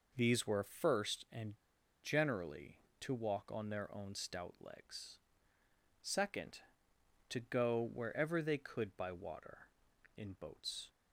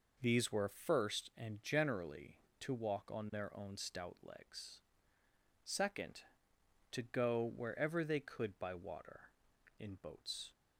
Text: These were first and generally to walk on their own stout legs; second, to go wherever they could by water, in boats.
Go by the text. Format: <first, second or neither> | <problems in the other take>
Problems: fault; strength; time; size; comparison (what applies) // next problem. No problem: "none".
second | pauses between "and" and "generally"; noticeable; at 1.5 s; 0.46 s long